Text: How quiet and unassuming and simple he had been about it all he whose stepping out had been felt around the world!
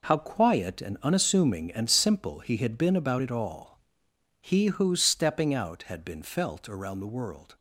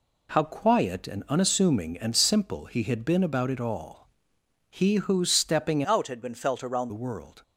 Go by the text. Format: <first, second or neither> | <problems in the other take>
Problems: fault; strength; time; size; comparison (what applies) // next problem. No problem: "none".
first | pauses between "all" and "he"; noticeable; at 4.0 s; 0.62 s long; noticeable in the first // changes voice from "out" to "around"; from 5.8 to 6.8 s; 1.0 s long